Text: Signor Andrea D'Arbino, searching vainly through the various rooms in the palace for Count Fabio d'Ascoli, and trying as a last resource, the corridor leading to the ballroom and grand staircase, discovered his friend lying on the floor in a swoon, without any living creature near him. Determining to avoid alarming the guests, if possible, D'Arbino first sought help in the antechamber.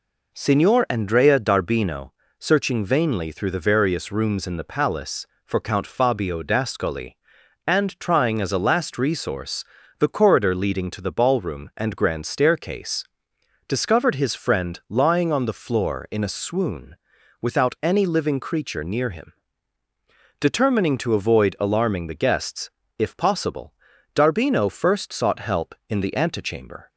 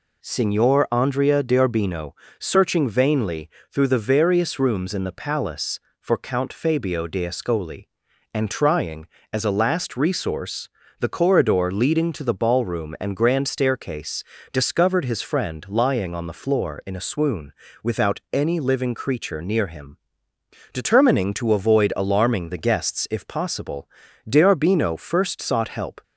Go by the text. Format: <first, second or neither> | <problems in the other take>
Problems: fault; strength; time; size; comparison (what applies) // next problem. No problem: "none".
first | pauses between "vainly" and "through"; slight; at 3.4 s; 0.24 s long // stops before "in the antechamber"; at 26.0 s